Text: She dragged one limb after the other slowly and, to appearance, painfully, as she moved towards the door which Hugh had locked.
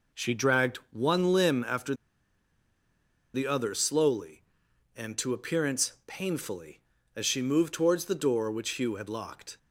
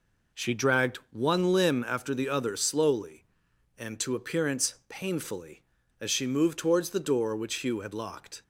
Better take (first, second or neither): second